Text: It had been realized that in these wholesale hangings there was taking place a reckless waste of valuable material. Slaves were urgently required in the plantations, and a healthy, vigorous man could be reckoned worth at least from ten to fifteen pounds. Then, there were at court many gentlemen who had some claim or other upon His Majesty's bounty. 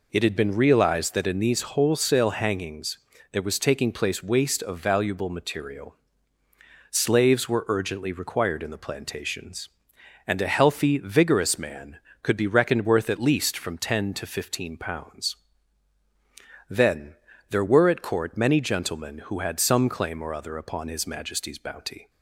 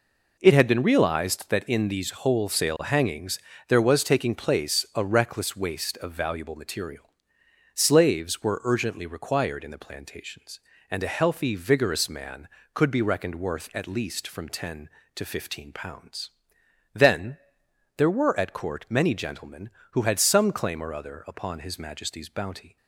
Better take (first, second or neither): second